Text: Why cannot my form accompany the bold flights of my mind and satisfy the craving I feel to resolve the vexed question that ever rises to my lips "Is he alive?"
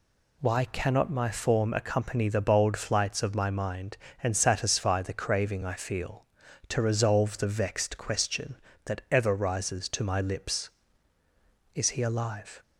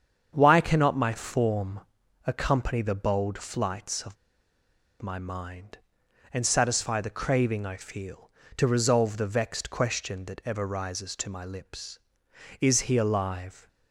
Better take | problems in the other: first | starts louder than the rest; strong; until 1.3 s; 7.5 dB // pauses between "form" and "accompany"; at 1.8 s; 0.44 s long // pauses between "of" and "my"; noticeable; at 4.1 s; 0.85 s long

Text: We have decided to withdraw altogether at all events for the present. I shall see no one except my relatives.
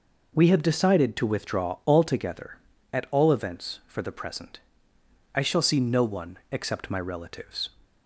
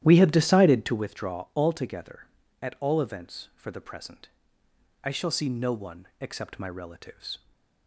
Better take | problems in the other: first | starts louder than the rest; strong; until 1.1 s; 12 dB // stays silent after the last word; slight; from 7.3 s on; 0.5 s long

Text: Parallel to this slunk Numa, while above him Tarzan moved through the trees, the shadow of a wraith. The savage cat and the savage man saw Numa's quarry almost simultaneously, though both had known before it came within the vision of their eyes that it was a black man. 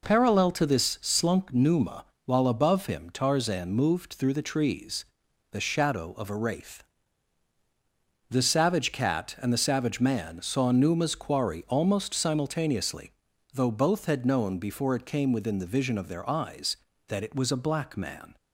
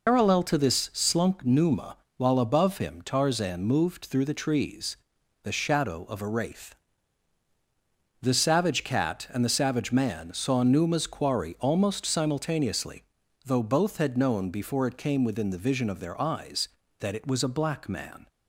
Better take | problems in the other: first | loses the start of "Parallel"; at 0.0 s; 120 ms

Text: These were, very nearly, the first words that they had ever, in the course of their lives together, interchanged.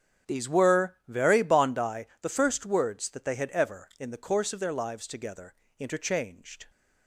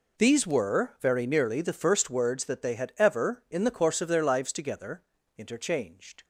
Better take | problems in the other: second | starts louder than the rest; strong; until 1.3 s; 8.5 dB // says "bondi" for "nearly"; at 1.4 s

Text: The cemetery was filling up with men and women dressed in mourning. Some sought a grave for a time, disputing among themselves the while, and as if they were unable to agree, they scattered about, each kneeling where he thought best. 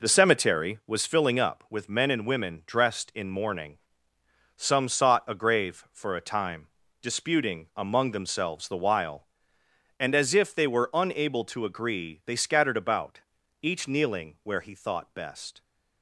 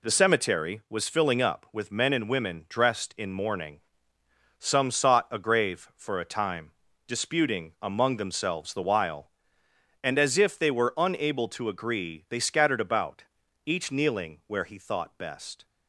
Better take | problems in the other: second | starts louder than the rest; noticeable; until 1.3 s; 4 dB

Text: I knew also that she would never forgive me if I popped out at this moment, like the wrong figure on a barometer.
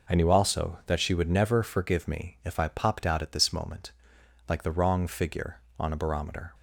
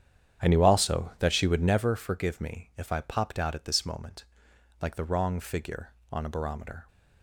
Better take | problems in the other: first | starts louder than the rest; strong; until 1.9 s; 9 dB

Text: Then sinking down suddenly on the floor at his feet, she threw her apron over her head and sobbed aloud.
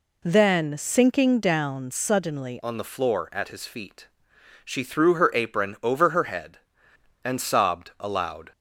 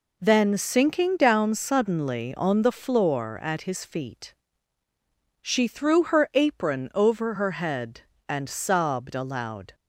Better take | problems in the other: second | changes voice at "on"; from 2.6 s on; 5.9 s long

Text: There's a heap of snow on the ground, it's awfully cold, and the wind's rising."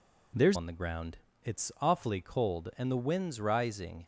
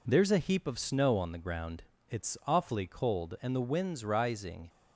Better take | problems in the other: second | skips "a heap of snow"; at 0.5 s

